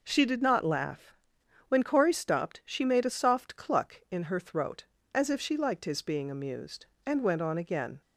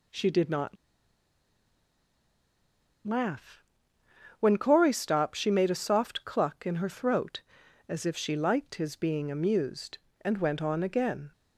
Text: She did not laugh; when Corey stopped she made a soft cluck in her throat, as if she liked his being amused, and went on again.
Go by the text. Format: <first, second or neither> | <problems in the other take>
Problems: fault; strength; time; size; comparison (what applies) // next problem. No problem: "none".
first | pauses between "not" and "laugh"; strong; at 0.7 s; 2.3 s long